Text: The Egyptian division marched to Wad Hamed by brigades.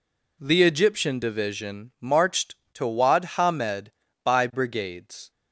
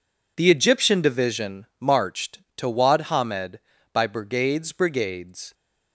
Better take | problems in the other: first | pauses between "division" and "marched"; slight; at 1.6 s; 0.16 s long // says "brigades" twice; at 4.7 s

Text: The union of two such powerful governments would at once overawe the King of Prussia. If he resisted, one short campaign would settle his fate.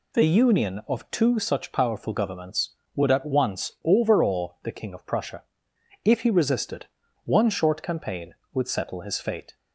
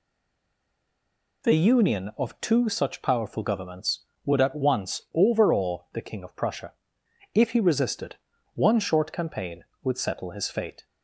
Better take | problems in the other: first | stays silent before the first word; noticeable; until 1.4 s; 1.4 s long

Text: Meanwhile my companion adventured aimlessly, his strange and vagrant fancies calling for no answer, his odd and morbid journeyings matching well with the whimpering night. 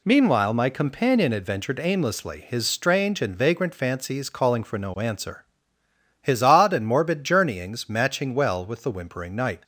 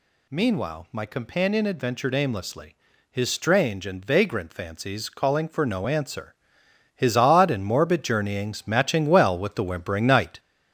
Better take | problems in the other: first | gets louder; noticeable; throughout; 5.5 dB

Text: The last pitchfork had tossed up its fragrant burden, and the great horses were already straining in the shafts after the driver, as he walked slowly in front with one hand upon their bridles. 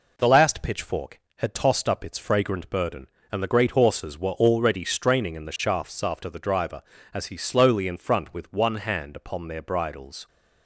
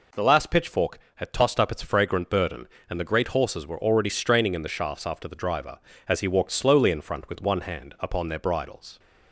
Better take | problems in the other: second | skips "walked"; at 7.3 s

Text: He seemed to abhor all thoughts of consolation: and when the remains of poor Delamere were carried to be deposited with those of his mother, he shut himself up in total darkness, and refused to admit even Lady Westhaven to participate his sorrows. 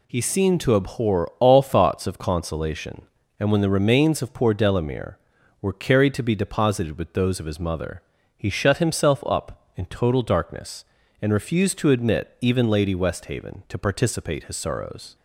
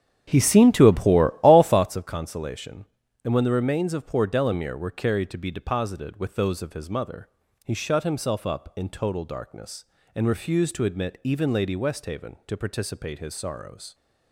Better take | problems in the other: first | starts louder than the rest; strong; until 1.9 s; 9 dB

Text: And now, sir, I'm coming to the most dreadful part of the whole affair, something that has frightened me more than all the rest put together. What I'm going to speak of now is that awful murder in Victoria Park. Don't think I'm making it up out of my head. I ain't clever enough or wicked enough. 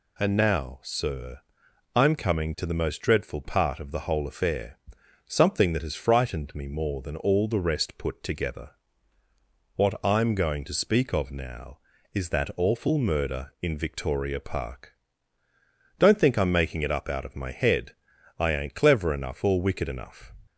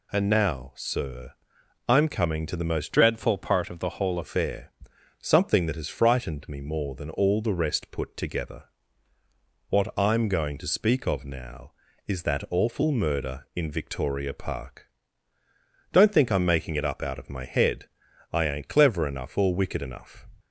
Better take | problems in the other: first | changes voice from "dreadful" to "whole"; from 2.9 to 4.1 s; 1.2 s long

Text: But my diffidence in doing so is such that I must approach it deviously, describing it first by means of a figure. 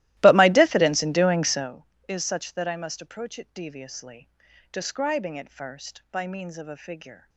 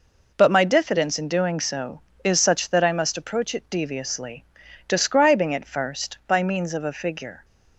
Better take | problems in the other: second | starts louder than the rest; strong; until 1.7 s; 16.5 dB

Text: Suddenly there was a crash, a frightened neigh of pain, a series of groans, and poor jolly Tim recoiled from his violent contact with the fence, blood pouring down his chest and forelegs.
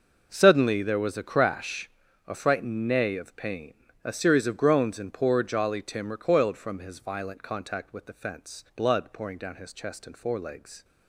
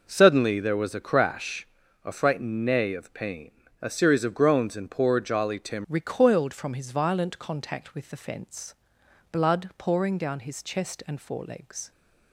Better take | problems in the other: first | changes voice at "recoiled"; from 5.8 s on; 6.1 s long

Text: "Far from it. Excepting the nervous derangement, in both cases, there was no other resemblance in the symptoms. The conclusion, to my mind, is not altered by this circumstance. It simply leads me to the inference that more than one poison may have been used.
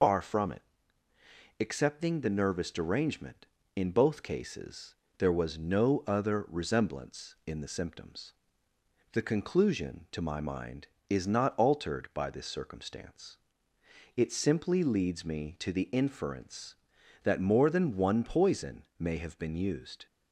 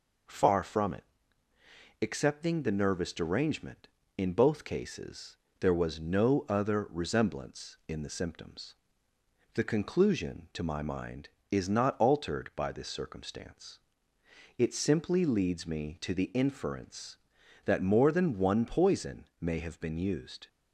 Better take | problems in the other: second | loses the start of "Far"; at 0.0 s; 145 ms // pauses between "poison" and "may"; slight; at 18.8 s; 0.16 s long; slight in the second

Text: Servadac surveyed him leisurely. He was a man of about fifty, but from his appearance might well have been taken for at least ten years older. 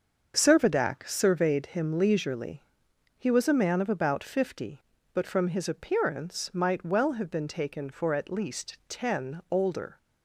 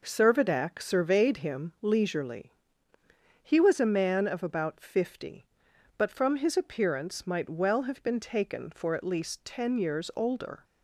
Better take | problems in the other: second | starts louder than the rest; until 1.3 s; 6.5 dB // skips "years"; at 9.4 s

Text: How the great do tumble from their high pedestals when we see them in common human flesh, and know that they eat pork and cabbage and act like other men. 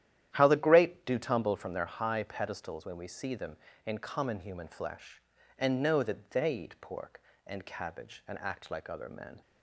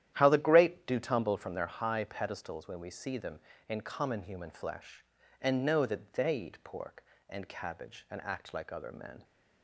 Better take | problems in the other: neither | starts louder than the rest; strong; the same in both

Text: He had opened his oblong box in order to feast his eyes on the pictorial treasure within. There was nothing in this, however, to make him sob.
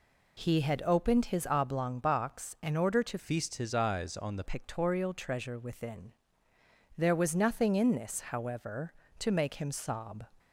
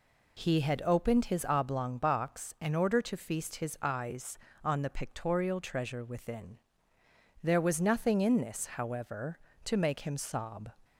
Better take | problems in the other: second | changes voice from "feast" to "the"; from 3.1 to 4.4 s; 1.3 s long

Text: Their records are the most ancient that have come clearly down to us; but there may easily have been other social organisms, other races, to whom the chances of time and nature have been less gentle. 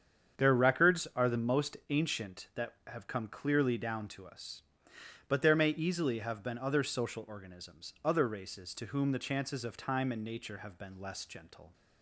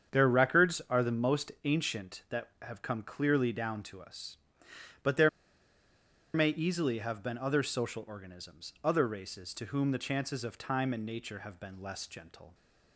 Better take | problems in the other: first | starts louder than the rest; strong; until 1.2 s; 7.5 dB; strong in the first // pauses between "there" and "may"; at 5.2 s; 1.0 s long

